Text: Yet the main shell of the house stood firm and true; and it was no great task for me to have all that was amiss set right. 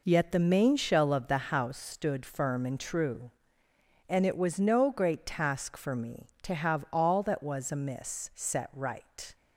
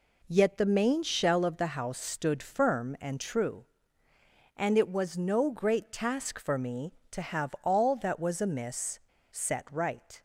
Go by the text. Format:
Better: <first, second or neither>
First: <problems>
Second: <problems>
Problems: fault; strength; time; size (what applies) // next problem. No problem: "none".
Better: first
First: none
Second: pauses between "amiss" and "set"; slight; at 8.9 s; 0.31 s long